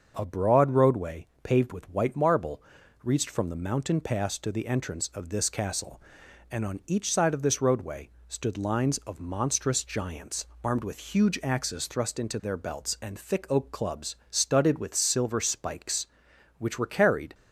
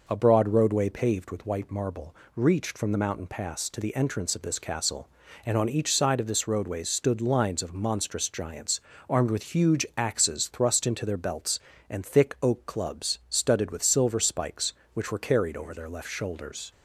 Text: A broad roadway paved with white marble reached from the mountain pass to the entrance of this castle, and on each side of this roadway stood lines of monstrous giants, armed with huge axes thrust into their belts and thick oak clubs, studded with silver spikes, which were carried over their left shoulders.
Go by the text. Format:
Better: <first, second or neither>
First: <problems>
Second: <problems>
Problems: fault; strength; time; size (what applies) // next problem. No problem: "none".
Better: second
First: starts louder than the rest; until 1.1 s; 6.5 dB // pauses between "roadway" and "paved"; slight; at 1.2 s; 0.16 s long // pauses between "marble" and "reached"; at 2.6 s; 0.42 s long // pauses between "roadway" and "stood"; slight; at 8.0 s; 0.20 s long // stops before "over their left shoulders"; at 17.3 s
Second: pauses between "marble" and "reached"; slight; at 2.1 s; 0.18 s long